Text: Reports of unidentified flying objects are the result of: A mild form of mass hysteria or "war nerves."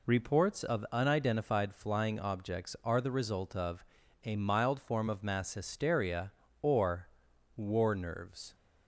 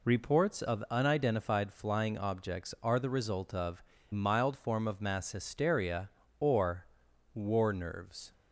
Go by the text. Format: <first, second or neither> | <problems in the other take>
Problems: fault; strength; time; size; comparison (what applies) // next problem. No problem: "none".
first | skips "A"; at 3.9 s // pauses between "or" and "war"; noticeable; at 6.8 s; 0.48 s long; noticeable in the first